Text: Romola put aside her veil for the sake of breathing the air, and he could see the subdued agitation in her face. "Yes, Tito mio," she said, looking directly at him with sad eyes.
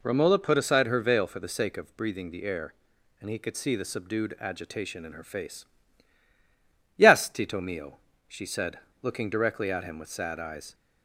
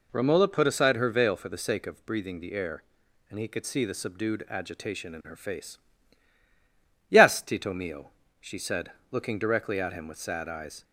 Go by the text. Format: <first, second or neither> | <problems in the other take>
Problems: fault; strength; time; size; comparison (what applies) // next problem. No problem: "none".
neither | none